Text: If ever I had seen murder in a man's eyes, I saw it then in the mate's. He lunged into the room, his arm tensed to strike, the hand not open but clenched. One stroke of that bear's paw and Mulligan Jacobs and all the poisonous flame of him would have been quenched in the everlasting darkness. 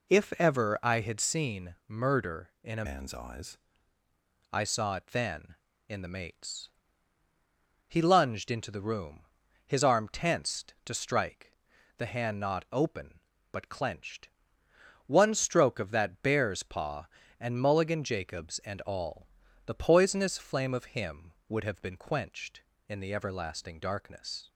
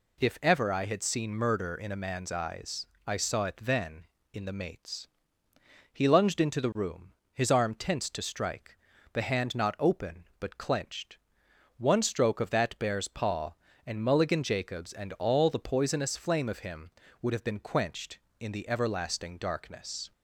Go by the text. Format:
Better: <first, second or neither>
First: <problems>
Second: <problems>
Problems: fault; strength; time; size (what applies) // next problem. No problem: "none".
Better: second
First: changes voice from "man's" to "eyes"; from 2.8 to 3.5 s; 0.7 s long // pauses between "all" and "the"; at 19.2 s; 0.40 s long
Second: none